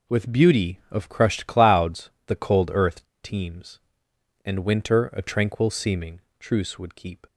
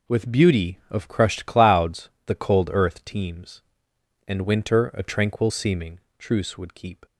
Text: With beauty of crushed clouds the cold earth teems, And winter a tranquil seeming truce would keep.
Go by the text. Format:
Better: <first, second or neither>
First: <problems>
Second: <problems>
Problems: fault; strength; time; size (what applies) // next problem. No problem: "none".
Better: second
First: pauses between "clouds" and "the"; slight; at 2.1 s; 0.16 s long // pauses between "earth" and "teems"; slight; at 3.0 s; 0.17 s long // pauses between "seeming" and "truce"; slight; at 6.2 s; 0.18 s long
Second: pauses between "clouds" and "the"; slight; at 2.1 s; 0.16 s long // pauses between "seeming" and "truce"; slight; at 5.9 s; 0.18 s long